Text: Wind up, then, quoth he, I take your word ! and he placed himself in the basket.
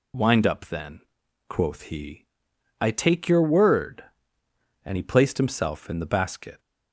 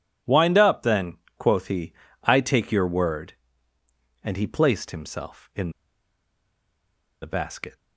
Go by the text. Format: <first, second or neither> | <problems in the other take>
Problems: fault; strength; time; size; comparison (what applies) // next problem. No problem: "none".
first | pauses between "in" and "the"; strong; at 5.6 s; 1.5 s long